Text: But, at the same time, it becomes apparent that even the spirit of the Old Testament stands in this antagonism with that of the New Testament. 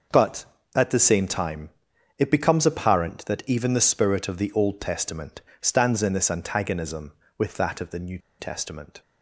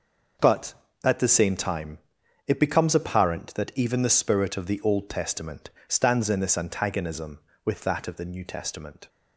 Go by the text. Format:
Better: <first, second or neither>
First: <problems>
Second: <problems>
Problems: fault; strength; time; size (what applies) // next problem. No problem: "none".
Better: second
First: pauses between "Testament" and "stands"; slight; at 5.4 s; 0.18 s long // pauses between "New" and "Testament"; slight; at 8.1 s; 0.21 s long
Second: pauses between "Testament" and "stands"; slight; at 5.7 s; 0.16 s long